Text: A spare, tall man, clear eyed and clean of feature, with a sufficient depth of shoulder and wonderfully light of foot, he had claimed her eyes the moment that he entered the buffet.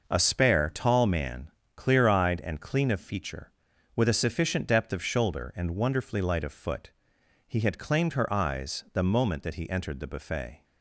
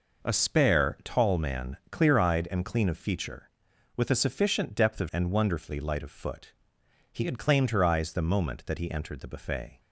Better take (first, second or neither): first